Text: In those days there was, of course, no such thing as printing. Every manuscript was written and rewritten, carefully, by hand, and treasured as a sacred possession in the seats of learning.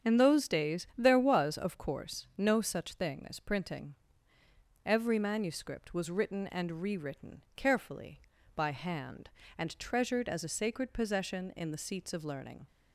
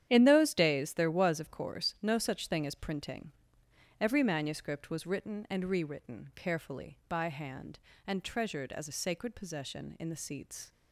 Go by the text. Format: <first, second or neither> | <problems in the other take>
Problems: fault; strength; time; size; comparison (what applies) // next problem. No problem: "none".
first | starts louder than the rest; strong; until 1.0 s; 10 dB; strong in the first // stops before "of learning"; at 10.7 s